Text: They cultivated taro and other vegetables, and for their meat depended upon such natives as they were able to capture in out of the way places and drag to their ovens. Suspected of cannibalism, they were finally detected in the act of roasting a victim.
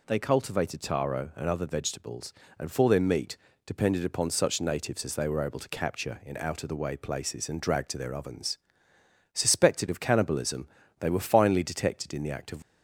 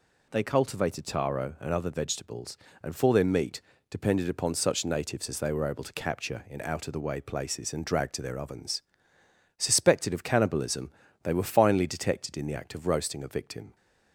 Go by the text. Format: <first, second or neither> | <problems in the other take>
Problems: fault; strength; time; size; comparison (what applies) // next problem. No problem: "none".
second | pauses between "meat" and "depended"; slight; at 3.3 s; 0.30 s long; slight in the second // stops before "roasting a victim"; at 12.6 s